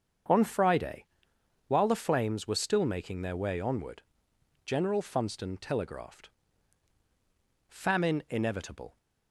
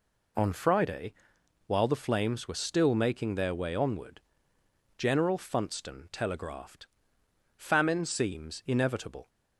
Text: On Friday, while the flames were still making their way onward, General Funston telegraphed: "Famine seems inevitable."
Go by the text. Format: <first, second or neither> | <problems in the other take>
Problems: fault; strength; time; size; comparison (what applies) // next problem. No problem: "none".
second | starts louder than the rest; strong; until 1.9 s; 7 dB // skips "seems"; at 8.2 s